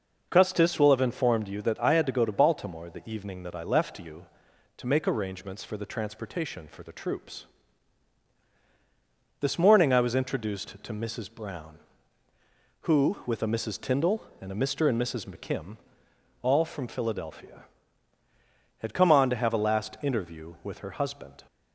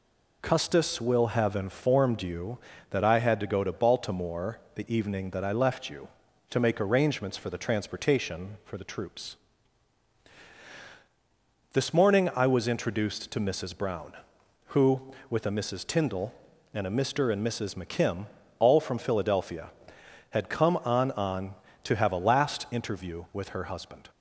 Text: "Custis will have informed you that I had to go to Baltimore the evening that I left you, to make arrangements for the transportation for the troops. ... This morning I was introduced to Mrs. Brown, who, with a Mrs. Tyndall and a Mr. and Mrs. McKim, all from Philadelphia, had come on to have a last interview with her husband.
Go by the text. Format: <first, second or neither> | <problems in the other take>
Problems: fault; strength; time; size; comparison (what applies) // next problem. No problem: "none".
first | pauses between "Baltimore" and "the"; slight; at 4.5 s; 0.16 s long // says "on" twice; at 21.1 s